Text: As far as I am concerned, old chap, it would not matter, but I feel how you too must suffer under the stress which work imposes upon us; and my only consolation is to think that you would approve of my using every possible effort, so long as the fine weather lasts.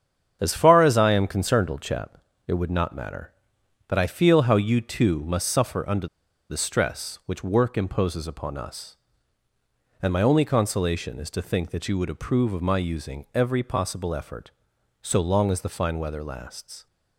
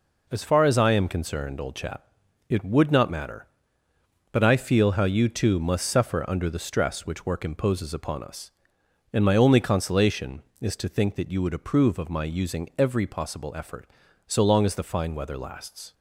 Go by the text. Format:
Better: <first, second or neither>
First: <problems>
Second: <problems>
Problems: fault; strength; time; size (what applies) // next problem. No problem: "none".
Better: second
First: starts louder than the rest; strong; until 1.4 s; 8 dB // pauses between "under" and "the"; at 6.0 s; 0.42 s long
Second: none